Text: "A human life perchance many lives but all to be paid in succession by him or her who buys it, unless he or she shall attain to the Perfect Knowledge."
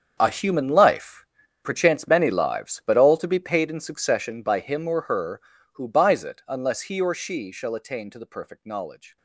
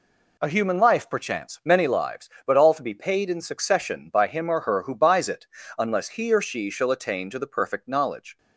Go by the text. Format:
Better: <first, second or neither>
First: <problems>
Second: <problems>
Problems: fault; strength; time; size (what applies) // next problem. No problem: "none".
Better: second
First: gets quieter; strong; throughout; 16.5 dB // pauses between "life" and "perchance"; at 1.2 s; 0.38 s long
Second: none